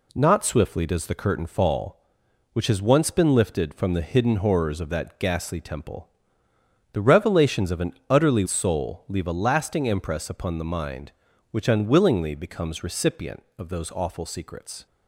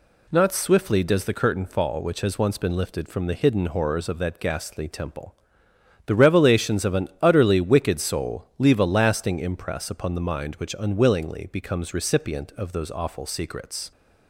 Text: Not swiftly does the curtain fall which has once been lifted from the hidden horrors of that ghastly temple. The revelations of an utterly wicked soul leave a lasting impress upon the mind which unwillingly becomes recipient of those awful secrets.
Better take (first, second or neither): second